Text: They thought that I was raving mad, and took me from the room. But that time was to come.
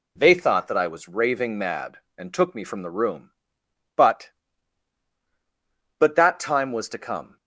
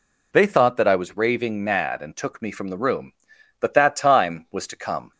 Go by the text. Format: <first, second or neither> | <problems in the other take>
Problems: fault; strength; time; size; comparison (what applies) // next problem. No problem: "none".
second | says "But" twice; at 5.9 s